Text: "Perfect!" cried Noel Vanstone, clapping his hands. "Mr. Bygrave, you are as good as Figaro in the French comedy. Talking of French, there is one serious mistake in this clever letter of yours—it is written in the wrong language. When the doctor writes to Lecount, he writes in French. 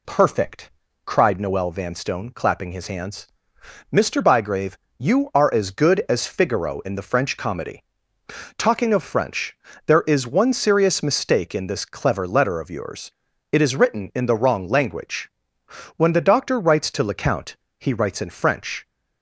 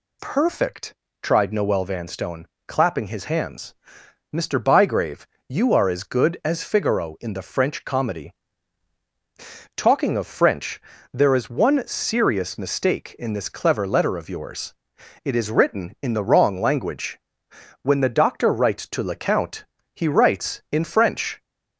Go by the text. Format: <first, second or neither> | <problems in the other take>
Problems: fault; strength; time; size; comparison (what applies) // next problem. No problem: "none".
first | says "tried" for "cried"; at 1.2 s